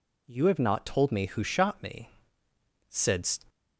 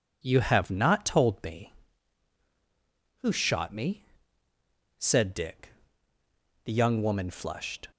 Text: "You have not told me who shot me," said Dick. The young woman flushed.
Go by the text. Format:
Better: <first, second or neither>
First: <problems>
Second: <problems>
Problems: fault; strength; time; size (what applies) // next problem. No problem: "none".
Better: second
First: stops before "Dick The young woman flushed"; at 3.4 s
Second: none